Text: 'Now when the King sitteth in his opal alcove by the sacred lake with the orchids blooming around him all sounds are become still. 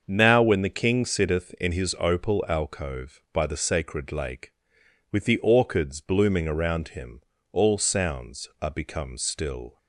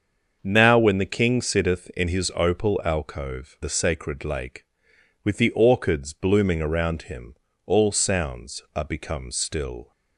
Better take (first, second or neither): first